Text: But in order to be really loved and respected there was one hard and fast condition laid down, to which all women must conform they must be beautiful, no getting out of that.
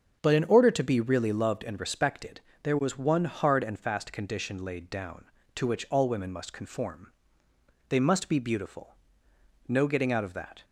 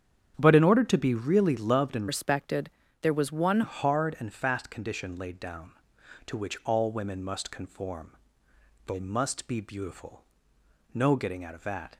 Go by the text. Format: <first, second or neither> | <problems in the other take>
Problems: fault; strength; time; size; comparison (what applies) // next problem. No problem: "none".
first | starts louder than the rest; strong; until 1.3 s; 9 dB; also in the first // changes voice from "respected" to "one"; from 2.0 to 3.6 s; 1.6 s long // pauses between "respected" and "there"; slight; at 2.6 s; 0.32 s long; slight in the first // pauses between "conform" and "they"; noticeable; at 8.1 s; 0.74 s long; noticeable in the first